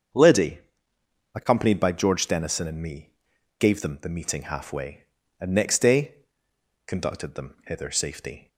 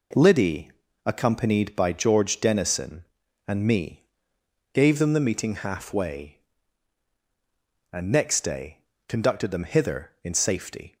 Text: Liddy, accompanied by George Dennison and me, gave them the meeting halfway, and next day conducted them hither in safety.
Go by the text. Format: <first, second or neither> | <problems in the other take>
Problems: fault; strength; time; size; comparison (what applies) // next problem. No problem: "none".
second | starts louder than the rest; until 1.9 s; 7 dB // pauses between "day" and "conducted"; noticeable; at 6.1 s; 0.74 s long; slight in the second // skips "in"; at 7.8 s